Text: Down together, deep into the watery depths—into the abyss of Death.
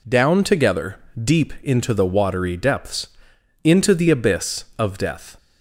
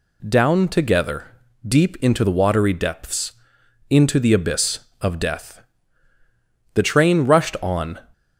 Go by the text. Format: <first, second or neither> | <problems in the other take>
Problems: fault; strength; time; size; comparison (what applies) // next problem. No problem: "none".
first | goes on to say "The train rushed on"; noticeable; from 6.7 s on; 1.2 s long